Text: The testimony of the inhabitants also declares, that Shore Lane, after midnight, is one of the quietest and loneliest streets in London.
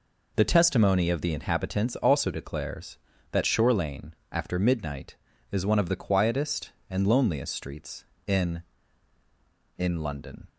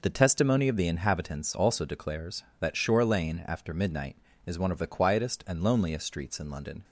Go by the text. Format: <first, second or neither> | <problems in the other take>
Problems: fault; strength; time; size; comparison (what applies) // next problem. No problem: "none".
second | says "in" twice; at 9.7 s